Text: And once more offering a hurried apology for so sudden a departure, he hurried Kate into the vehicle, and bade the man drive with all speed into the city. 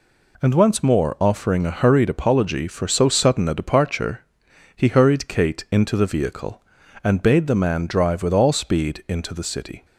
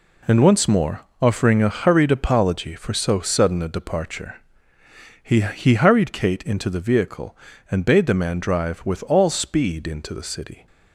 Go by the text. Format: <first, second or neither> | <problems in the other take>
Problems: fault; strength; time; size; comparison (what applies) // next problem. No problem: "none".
first | pauses between "more" and "offering"; slight; at 1.0 s; 0.20 s long // says "he" twice; at 5.4 s